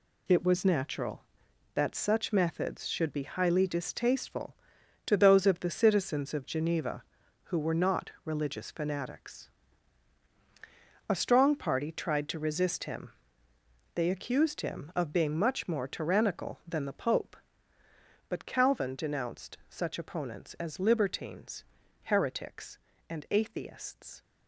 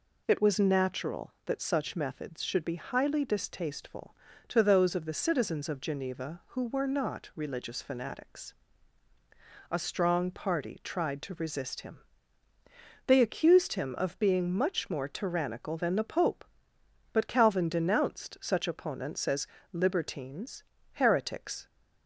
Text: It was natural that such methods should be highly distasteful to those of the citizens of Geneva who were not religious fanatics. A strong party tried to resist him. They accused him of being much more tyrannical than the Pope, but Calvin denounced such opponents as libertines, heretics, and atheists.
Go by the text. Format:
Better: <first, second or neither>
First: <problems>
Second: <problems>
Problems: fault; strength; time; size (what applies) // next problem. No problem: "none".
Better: first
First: none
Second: pauses between "as" and "libertines"; slight; at 19.4 s; 0.28 s long // stops before "and atheists"; at 21.6 s